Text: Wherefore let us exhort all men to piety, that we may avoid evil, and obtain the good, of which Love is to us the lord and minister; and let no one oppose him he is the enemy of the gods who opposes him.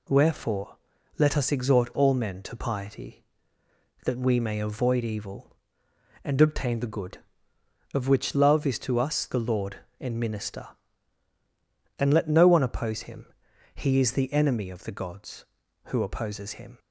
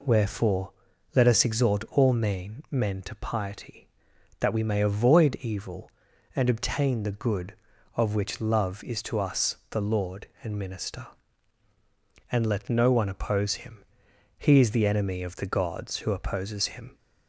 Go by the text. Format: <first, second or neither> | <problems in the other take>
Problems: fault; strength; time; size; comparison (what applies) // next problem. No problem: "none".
first | pauses between "Wherefore" and "let"; at 0.7 s; 0.42 s long; also in the first // says "men" twice; at 2.7 s // pauses between "him" and "he"; noticeable; at 13.8 s; 0.56 s long; noticeable in the first